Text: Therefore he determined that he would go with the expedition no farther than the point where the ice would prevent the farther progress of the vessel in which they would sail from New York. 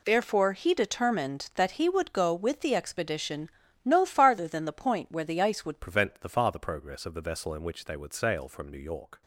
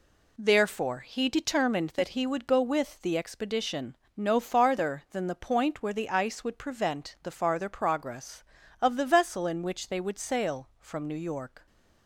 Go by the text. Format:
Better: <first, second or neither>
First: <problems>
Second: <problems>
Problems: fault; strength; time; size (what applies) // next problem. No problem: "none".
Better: second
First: pauses between "expedition" and "no"; slight; at 3.4 s; 0.34 s long // changes voice at "prevent"; from 5.8 s on; 3.4 s long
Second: pauses between "expedition" and "no"; slight; at 3.9 s; 0.20 s long